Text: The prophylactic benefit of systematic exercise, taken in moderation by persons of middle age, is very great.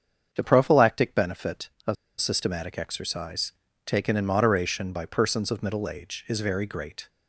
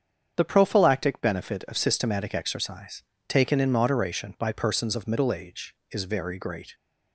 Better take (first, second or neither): second